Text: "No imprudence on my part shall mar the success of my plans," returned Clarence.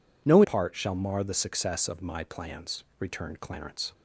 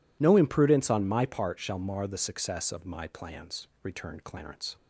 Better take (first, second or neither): second